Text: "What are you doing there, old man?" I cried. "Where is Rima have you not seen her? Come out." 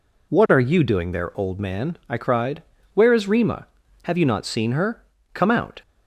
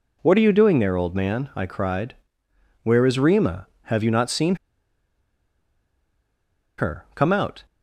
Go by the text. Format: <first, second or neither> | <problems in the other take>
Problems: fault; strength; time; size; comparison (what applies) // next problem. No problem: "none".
first | pauses between "seen" and "her"; strong; at 4.5 s; 2.2 s long